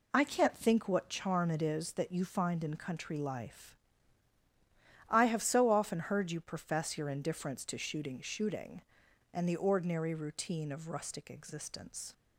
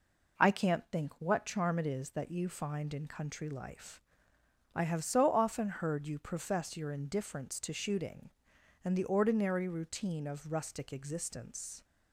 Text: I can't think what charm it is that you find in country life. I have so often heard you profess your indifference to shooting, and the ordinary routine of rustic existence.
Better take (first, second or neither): second